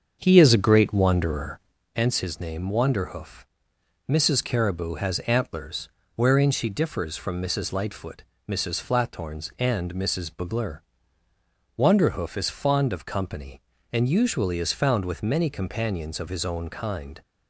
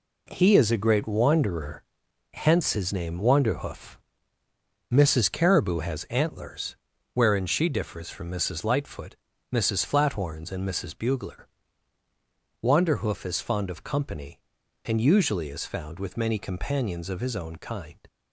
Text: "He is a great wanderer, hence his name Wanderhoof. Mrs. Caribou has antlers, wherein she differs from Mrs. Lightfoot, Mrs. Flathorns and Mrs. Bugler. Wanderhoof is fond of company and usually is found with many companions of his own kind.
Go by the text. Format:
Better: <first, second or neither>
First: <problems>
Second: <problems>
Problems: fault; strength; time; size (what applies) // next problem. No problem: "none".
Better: second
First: starts louder than the rest; until 1.8 s; 7 dB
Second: none